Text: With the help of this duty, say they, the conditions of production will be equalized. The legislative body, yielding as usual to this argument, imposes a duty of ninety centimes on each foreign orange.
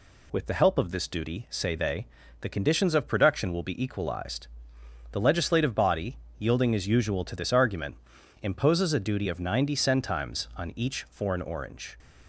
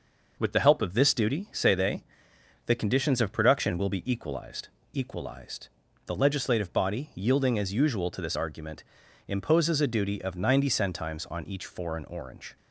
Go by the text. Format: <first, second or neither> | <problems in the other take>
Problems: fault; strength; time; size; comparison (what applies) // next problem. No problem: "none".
first | says "equalized" twice; at 4.9 s